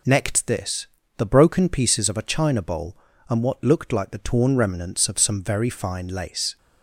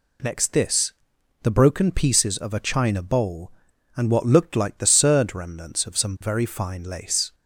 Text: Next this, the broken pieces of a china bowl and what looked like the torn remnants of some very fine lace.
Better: first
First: none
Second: says "surd" for "torn"; at 4.8 s

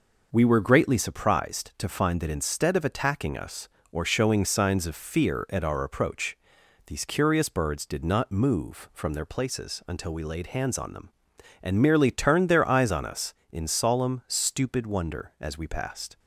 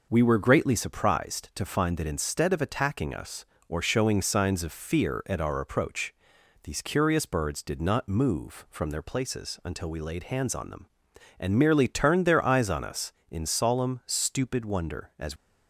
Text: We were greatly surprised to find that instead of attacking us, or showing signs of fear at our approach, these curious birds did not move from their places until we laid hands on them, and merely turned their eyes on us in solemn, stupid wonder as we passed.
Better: first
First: none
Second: stops before "we passed"; at 15.3 s

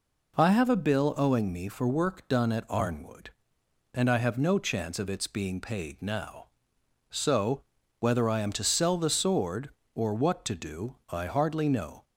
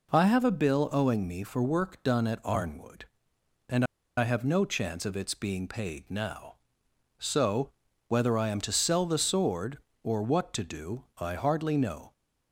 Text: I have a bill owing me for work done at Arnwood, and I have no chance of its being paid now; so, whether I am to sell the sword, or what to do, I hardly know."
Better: first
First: none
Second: pauses between "and" and "I"; slight; at 3.8 s; 0.31 s long

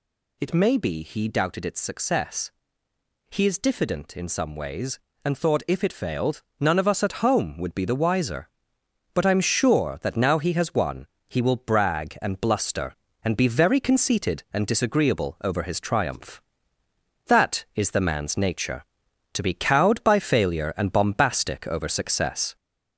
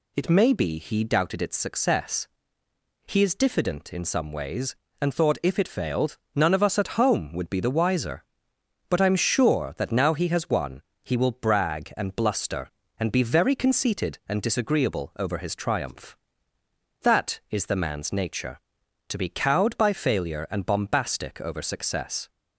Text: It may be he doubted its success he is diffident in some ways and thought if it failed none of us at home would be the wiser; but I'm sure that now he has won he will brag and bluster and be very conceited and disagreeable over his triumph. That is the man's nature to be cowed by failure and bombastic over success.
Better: second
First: gets louder; slight; throughout; 3 dB // pauses between "success" and "he"; noticeable; at 2.5 s; 0.80 s long // pauses between "failed" and "none"; slight; at 6.4 s; 0.16 s long // pauses between "won" and "he"; slight; at 11.0 s; 0.20 s long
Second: pauses between "success" and "he"; noticeable; at 2.2 s; 0.80 s long // pauses between "failed" and "none"; slight; at 6.1 s; 0.16 s long // pauses between "won" and "he"; slight; at 10.8 s; 0.20 s long

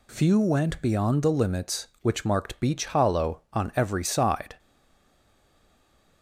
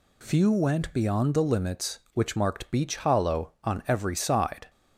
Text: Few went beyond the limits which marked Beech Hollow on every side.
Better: second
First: stays silent after the last word; noticeable; from 4.5 s on; 1.7 s long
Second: none

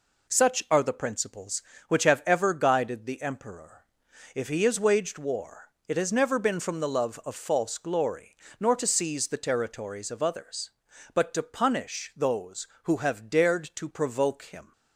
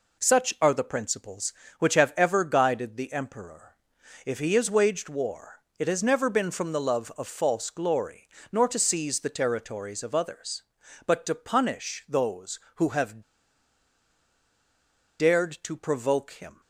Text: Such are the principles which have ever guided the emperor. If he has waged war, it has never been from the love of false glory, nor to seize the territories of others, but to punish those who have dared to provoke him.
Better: first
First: none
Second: pauses between "have" and "dared"; strong; at 13.2 s; 1.9 s long

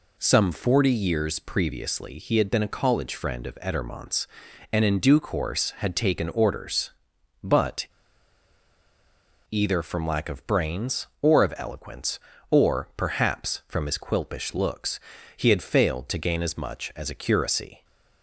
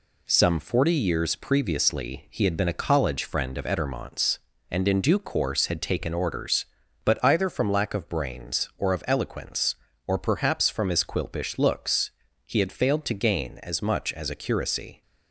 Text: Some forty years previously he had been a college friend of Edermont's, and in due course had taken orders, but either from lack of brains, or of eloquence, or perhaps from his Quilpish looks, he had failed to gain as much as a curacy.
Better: second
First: pauses between "but" and "either"; strong; at 7.8 s; 1.6 s long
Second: none

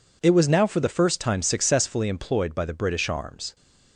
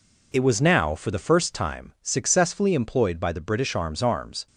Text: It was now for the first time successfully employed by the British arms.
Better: first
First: none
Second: says "arms" twice; at 4.0 s

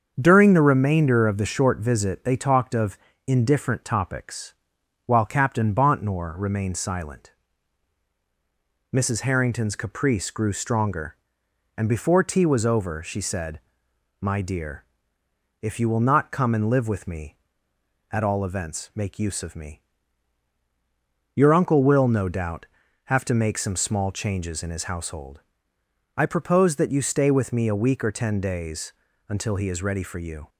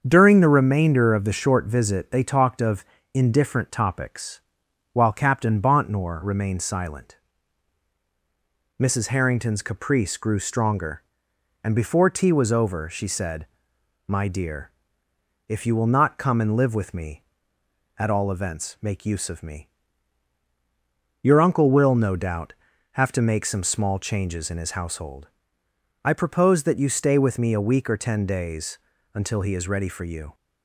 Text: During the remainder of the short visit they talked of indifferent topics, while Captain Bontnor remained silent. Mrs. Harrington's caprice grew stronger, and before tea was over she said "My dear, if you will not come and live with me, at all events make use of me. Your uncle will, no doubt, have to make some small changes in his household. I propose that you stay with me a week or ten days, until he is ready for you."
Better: neither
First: starts louder than the rest; until 1.1 s; 7 dB // pauses between "of" and "indifferent"; slight; at 2.9 s; 0.30 s long // pauses between "said" and "My"; noticeable; at 13.5 s; 0.62 s long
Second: starts louder than the rest; until 1.0 s; 7 dB // pauses between "of" and "indifferent"; slight; at 2.8 s; 0.30 s long // pauses between "said" and "My"; noticeable; at 13.4 s; 0.62 s long

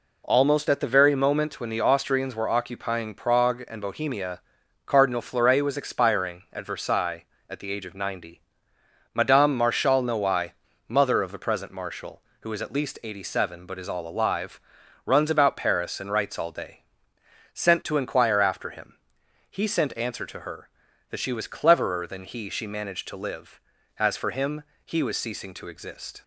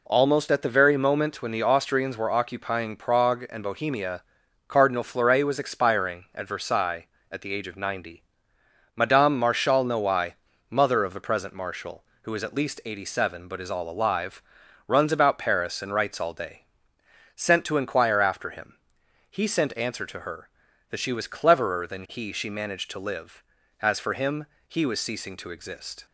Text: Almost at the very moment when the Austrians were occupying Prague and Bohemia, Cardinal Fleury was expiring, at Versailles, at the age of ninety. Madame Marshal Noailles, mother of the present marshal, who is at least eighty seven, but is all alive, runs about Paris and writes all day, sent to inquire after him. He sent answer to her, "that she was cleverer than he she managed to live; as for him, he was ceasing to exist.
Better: neither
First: none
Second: none

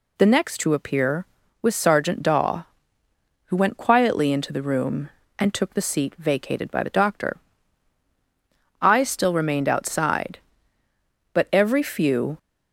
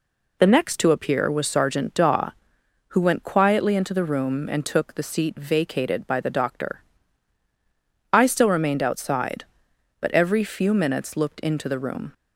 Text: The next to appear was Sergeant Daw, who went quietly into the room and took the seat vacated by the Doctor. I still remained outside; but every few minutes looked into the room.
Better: second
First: stops before "minutes looked into the room"; at 12.3 s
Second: none

